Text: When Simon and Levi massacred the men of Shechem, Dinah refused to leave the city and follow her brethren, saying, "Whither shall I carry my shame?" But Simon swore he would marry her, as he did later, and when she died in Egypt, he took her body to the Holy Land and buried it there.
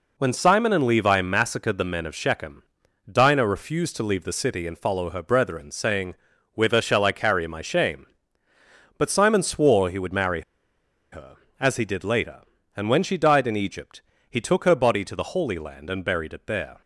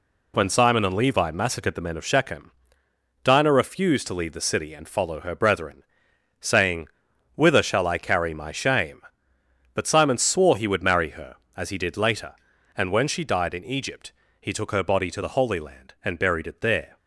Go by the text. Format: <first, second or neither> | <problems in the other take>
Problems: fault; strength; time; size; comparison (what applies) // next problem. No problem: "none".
second | pauses between "marry" and "her"; noticeable; at 10.4 s; 0.71 s long